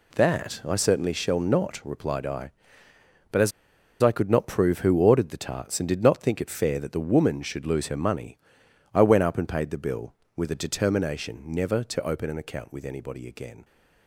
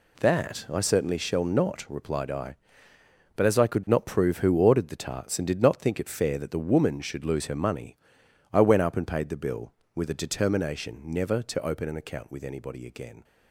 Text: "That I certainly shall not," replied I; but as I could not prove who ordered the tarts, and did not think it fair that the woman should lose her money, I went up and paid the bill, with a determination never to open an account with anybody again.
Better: second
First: pauses between "as" and "I"; noticeable; at 3.5 s; 0.51 s long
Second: none

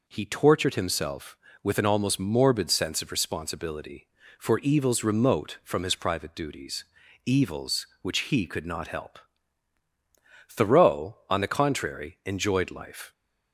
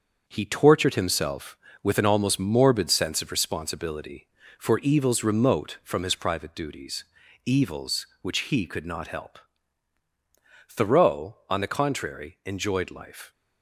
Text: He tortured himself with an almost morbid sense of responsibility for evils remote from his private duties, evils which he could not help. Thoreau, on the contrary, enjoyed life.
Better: first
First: none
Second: gets quieter; throughout; 6.5 dB

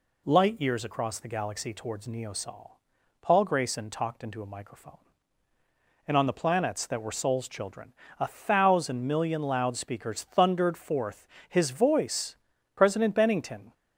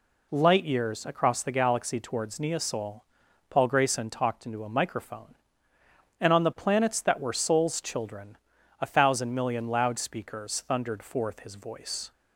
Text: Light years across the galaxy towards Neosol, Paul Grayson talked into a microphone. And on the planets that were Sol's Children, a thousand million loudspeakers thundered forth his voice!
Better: second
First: pauses between "forth" and "his"; slight; at 11.2 s; 0.22 s long // goes on to say "President Bennington"; noticeable; from 12.7 s on; 1.0 s long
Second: none

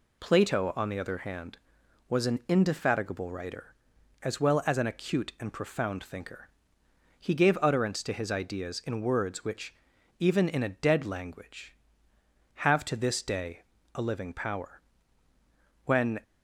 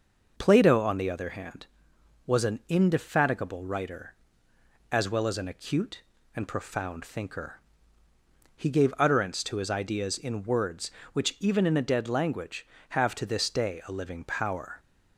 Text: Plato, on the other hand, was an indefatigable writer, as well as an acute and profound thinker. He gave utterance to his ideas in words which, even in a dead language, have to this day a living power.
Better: second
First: pauses between "day" and "a"; slight; at 13.6 s; 0.32 s long // goes on to say "When"; slight; from 15.8 s on; 0.36 s long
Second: none

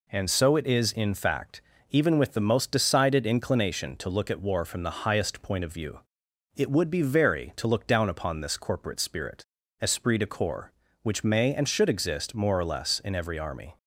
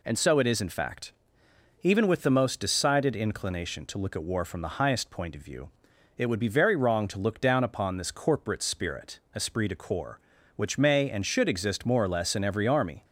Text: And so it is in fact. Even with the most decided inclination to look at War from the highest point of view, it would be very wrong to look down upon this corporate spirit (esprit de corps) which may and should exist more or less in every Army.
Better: second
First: skips "wrong"; at 7.5 s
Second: none

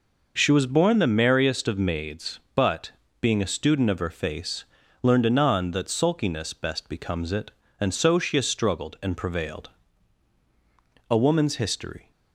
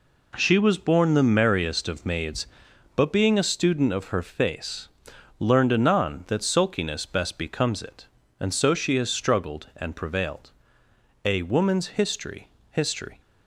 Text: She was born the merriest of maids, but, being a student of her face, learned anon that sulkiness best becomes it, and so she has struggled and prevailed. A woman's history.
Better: first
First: none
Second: says "history" twice; at 12.7 s

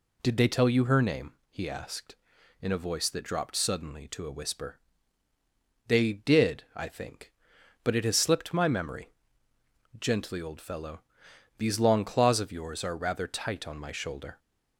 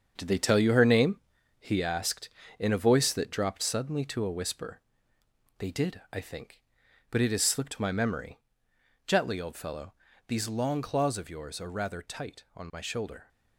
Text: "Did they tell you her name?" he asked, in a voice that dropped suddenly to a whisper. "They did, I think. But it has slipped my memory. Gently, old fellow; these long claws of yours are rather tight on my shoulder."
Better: first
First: none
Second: gets quieter; strong; throughout; 8 dB

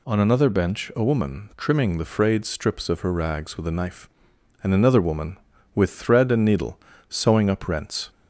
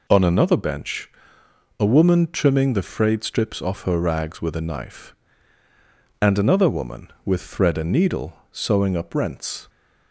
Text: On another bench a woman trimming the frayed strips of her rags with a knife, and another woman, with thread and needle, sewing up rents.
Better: first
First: none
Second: pauses between "bench" and "a"; noticeable; at 1.1 s; 0.70 s long // says "off" for "of"; at 3.6 s

